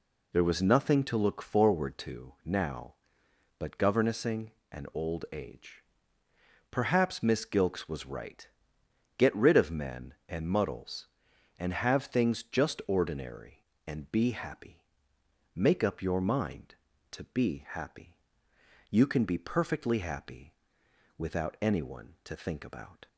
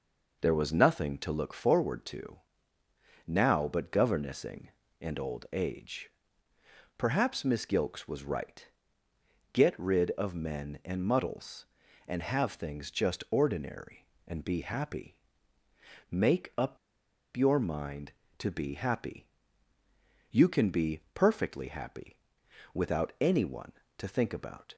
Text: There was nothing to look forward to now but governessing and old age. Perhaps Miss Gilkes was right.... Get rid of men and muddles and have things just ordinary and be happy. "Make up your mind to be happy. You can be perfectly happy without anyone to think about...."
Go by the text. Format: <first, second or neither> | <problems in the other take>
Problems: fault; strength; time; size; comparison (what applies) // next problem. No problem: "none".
first | pauses between "to" and "now"; noticeable; at 2.3 s; 0.88 s long // pauses between "up" and "your"; noticeable; at 16.7 s; 0.58 s long // pauses between "happy" and "without"; noticeable; at 22.1 s; 0.58 s long; noticeable in the first